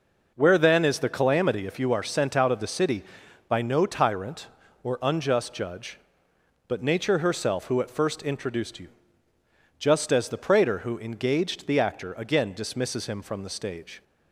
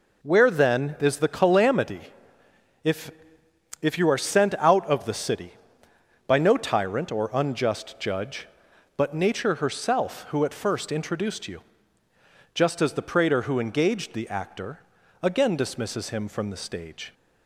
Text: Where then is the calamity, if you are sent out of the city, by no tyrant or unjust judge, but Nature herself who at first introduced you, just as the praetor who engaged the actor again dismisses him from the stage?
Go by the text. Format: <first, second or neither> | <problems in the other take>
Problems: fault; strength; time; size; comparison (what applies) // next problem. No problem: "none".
first | says "if" twice; at 3.8 s // pauses between "actor" and "again"; at 14.8 s; 0.42 s long